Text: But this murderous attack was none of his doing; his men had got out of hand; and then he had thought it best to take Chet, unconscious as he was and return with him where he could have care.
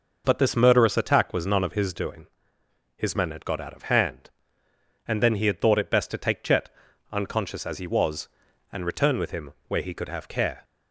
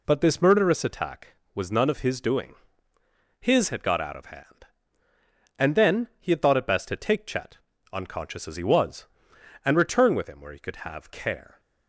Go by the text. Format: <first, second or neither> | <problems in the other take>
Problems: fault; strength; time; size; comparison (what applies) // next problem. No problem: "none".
first | skips "men"; at 3.6 s